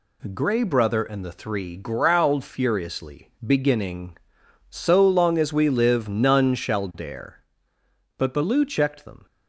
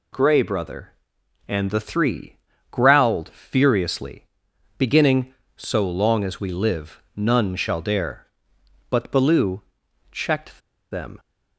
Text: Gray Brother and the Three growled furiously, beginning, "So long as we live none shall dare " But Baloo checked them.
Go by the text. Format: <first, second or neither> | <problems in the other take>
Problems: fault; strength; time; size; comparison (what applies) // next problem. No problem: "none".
first | pauses between "Three" and "growled"; slight; at 2.3 s; 0.32 s long // pauses between "Baloo" and "checked"; noticeable; at 9.6 s; 0.50 s long // pauses between "checked" and "them"; slight; at 10.5 s; 0.31 s long